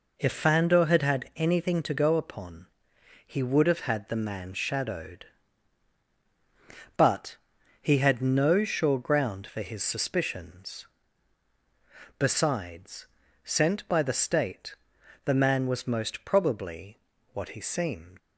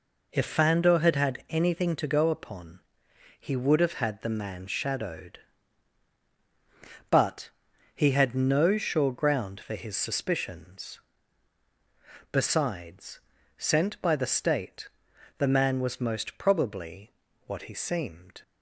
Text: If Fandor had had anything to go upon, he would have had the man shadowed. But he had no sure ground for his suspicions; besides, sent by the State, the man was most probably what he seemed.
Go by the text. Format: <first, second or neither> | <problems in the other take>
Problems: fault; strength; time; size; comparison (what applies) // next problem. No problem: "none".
second | pauses between "But" and "he"; at 7.3 s; 0.44 s long; also in the second // pauses between "probably" and "what"; slight; at 17.0 s; 0.32 s long; slight in the second // leaves "seemed" unfinished; at 18.1 s; 85 ms